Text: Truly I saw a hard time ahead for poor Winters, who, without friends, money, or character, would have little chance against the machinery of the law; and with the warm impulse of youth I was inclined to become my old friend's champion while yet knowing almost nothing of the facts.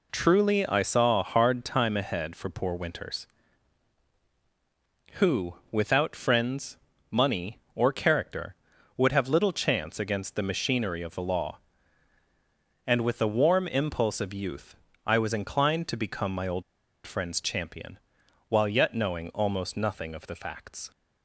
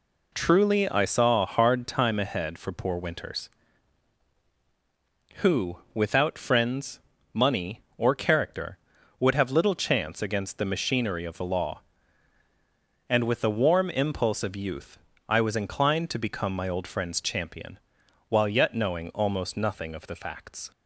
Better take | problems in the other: second | pauses between "youth" and "I"; slight; at 14.7 s; 0.32 s long; slight in the second // pauses between "old" and "friend's"; at 16.6 s; 0.43 s long // pauses between "champion" and "while"; noticeable; at 17.9 s; 0.50 s long; noticeable in the second

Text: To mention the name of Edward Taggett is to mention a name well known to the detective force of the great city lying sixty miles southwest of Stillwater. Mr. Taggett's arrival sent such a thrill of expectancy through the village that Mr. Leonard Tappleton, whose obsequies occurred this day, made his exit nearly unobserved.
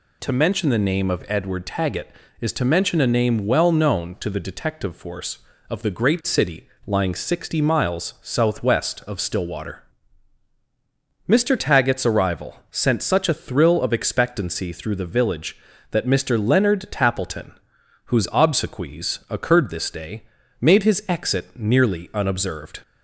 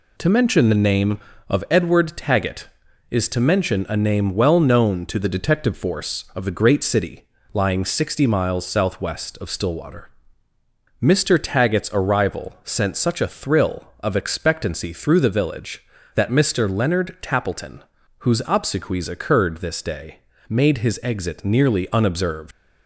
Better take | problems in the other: first | pauses between "city" and "lying"; slight; at 7.2 s; 0.26 s long; slight in the first // leaves "unobserved" unfinished; at 22.5 s; 105 ms

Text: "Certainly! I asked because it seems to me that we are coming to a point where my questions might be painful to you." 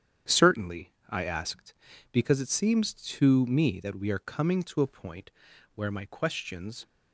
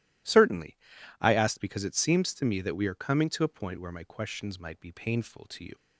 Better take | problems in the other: second | starts louder than the rest; strong; until 1.4 s; 9 dB // pauses between "point" and "where"; at 5.3 s; 0.44 s long // stops before "might be painful to you"; at 6.8 s

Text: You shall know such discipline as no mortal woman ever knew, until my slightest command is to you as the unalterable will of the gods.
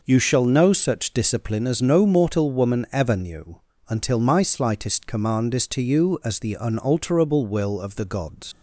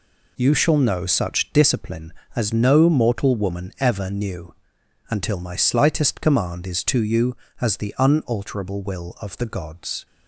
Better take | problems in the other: second | leaves "gods" unfinished; at 8.5 s; 95 ms

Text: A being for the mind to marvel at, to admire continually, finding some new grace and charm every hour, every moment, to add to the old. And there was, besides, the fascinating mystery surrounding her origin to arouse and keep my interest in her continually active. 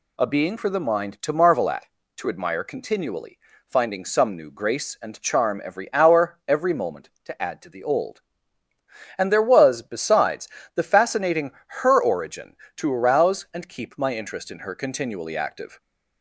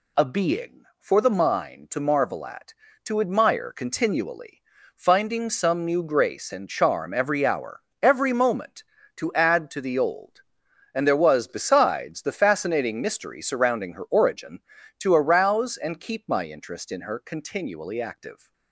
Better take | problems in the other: second | skips "mystery surrounding"; at 11.5 s

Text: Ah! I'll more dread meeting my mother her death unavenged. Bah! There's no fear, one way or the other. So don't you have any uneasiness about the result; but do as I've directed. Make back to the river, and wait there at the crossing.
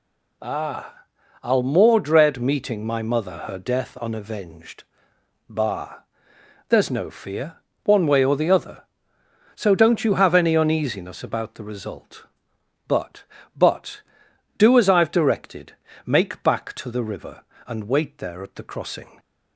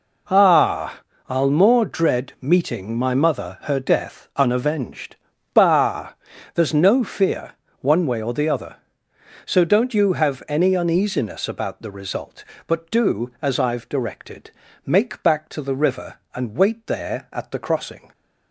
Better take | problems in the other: second | says "but" twice; at 13.5 s

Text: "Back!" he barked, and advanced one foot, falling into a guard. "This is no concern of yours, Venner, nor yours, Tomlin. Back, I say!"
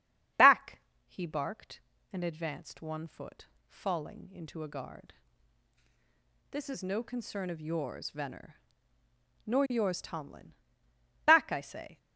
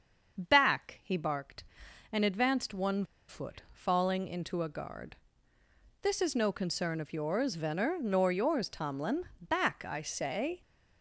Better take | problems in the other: first | starts louder than the rest; until 1.4 s; 6.5 dB; strong in the first // pauses between "one" and "foot"; slight; at 3.0 s; 0.23 s long

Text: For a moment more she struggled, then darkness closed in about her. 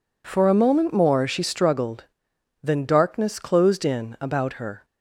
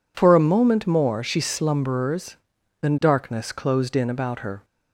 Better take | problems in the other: first | says "slumberers" for "struggled"; at 1.4 s

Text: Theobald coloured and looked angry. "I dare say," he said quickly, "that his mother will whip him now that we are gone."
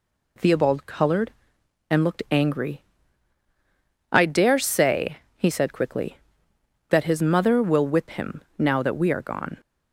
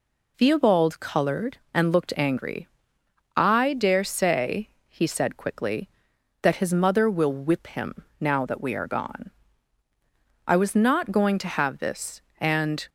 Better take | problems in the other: first | pauses between "him" and "now"; slight; at 8.0 s; 0.16 s long; slight in the first // goes on to say "I was not going to have this and"; strong; from 10.4 s on; 2.4 s long

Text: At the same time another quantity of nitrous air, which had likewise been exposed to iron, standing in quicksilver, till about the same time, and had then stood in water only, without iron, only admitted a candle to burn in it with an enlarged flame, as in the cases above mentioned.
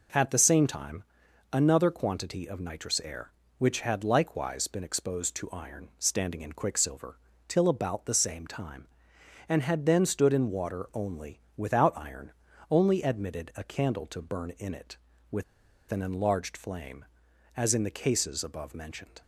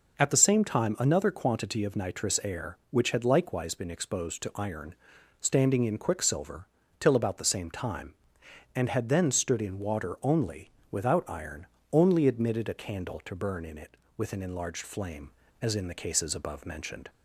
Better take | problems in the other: second | pauses between "time" and "another"; noticeable; at 1.0 s; 0.48 s long // pauses between "with" and "an"; noticeable; at 15.4 s; 0.47 s long

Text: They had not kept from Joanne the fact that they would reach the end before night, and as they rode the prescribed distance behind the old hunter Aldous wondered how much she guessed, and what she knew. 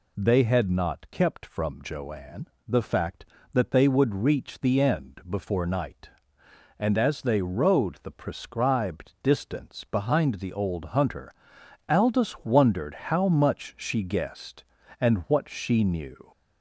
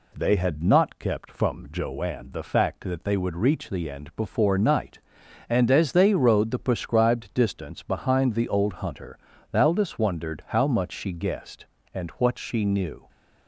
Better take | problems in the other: second | gets louder; slight; throughout; 3 dB // pauses between "Joanne" and "the"; slight; at 2.4 s; 0.22 s long // pauses between "hunter" and "Aldous"; noticeable; at 11.3 s; 0.56 s long; slight in the second

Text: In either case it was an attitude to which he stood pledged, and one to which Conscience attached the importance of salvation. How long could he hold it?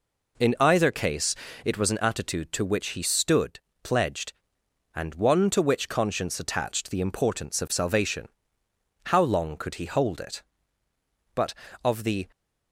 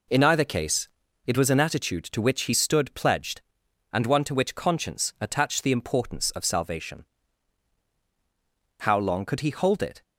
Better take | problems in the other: second | pauses between "case" and "it"; slight; at 1.3 s; 0.30 s long; also in the second // pauses between "stood" and "pledged"; slight; at 3.5 s; 0.24 s long // goes on to say "But of the"; noticeable; from 11.3 s on; 0.94 s long

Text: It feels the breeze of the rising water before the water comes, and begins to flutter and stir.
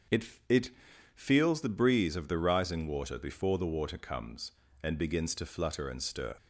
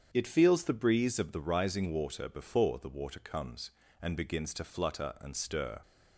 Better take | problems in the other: second | starts louder than the rest; until 1.7 s; 7 dB; strong in the second // says "It" twice; at 0.4 s

